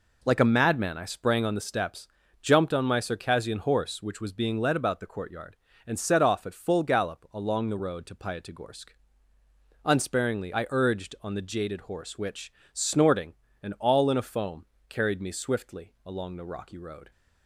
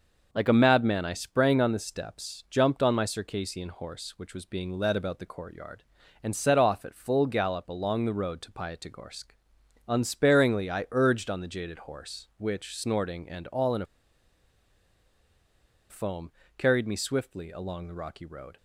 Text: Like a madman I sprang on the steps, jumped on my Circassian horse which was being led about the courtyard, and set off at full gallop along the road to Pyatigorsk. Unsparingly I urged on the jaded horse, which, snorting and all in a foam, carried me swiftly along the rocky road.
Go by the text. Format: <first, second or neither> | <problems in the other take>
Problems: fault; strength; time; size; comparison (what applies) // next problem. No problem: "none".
first | pauses between "a" and "foam"; strong; at 13.8 s; 2.0 s long